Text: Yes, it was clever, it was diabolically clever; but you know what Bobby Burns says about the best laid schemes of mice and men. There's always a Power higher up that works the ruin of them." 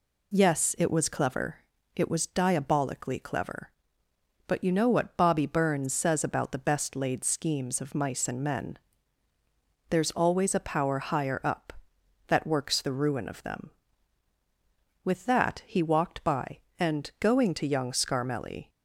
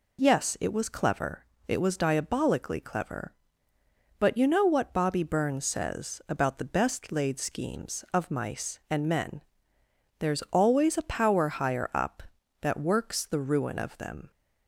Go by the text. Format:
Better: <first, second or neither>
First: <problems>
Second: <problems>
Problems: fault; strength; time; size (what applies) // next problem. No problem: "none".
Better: second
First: goes on to say "With that he walked by and going to young Scarmelli"; strong; from 15.0 s on; 3.6 s long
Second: none